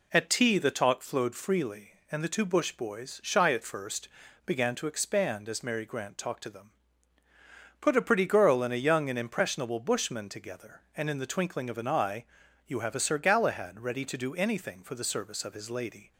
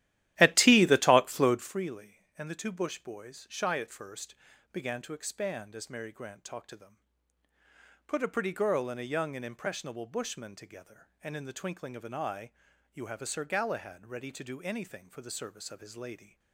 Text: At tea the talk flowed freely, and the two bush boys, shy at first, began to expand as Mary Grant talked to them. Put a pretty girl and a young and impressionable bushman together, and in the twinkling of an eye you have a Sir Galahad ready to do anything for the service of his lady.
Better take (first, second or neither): first